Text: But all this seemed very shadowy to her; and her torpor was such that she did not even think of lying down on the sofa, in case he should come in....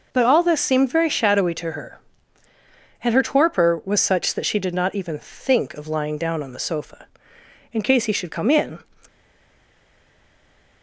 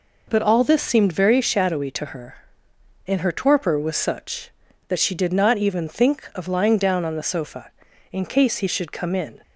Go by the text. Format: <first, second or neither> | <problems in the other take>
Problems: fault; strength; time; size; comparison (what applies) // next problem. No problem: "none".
second | stays silent after the last word; noticeable; from 9.0 s on; 1.8 s long